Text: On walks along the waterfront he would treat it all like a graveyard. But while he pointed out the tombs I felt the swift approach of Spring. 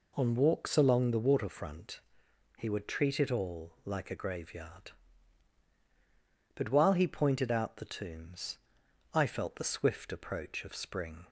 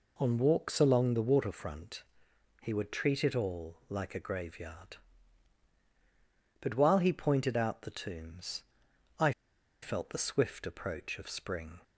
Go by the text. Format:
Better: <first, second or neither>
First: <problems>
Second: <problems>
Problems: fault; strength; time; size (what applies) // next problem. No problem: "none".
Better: first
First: pauses between "waterfront" and "he"; noticeable; at 1.9 s; 0.60 s long // pauses between "tombs" and "I"; noticeable; at 8.5 s; 0.56 s long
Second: pauses between "waterfront" and "he"; noticeable; at 2.0 s; 0.62 s long // pauses between "tombs" and "I"; noticeable; at 8.6 s; 0.56 s long // pauses between "I" and "felt"; noticeable; at 9.3 s; 0.51 s long